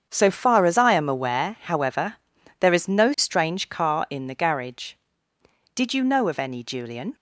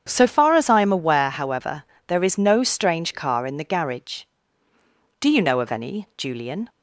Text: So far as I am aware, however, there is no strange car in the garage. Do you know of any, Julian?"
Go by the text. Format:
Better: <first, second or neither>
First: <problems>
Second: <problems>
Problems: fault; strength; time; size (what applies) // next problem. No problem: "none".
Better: second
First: starts louder than the rest; strong; until 1.1 s; 7.5 dB // says "Did" for "Do"; at 5.7 s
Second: starts louder than the rest; strong; until 1.0 s; 8 dB